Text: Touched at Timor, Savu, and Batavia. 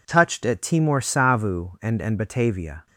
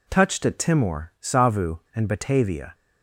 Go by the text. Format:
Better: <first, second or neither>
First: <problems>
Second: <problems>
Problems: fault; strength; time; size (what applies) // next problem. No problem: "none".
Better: second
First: says "and" twice; at 2.0 s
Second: none